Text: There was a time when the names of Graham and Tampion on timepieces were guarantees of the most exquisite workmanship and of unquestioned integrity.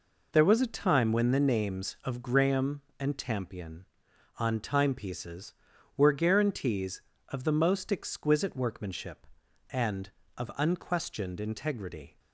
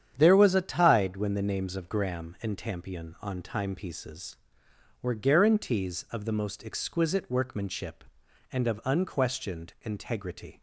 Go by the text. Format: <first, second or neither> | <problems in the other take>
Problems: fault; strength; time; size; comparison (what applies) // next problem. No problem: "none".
first | starts louder than the rest; strong; until 1.1 s; 9 dB // says "tide" for "time"; at 0.6 s